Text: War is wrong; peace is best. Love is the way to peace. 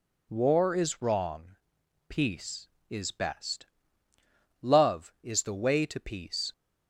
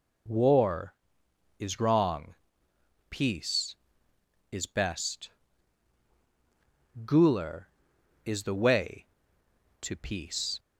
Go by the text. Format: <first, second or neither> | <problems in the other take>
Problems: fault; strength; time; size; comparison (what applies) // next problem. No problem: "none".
first | says "Guler" for "Love"; at 7.0 s